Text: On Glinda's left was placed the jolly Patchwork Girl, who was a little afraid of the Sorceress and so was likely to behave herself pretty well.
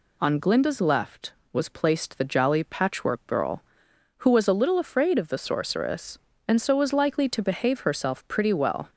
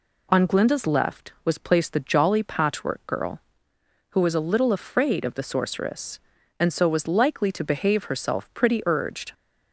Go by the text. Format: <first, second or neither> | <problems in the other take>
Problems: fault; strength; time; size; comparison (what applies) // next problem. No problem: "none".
first | says "urged" for "well"; at 8.8 s